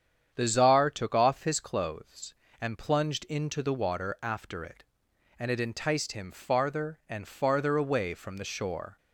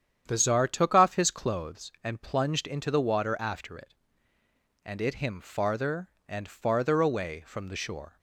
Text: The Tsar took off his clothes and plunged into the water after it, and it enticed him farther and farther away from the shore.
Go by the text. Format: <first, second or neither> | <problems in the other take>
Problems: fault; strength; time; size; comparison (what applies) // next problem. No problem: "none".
first | starts louder than the rest; strong; until 1.2 s; 9 dB; strong in the first // skips "enticed"; at 5.1 s